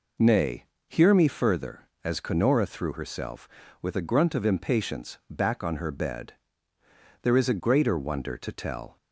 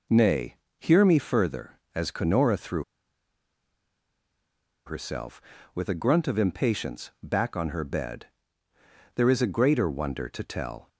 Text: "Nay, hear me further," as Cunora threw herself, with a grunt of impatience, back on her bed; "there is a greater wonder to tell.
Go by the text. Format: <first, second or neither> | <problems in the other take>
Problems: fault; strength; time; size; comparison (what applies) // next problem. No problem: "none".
first | pauses between "threw" and "herself"; strong; at 2.8 s; 2.0 s long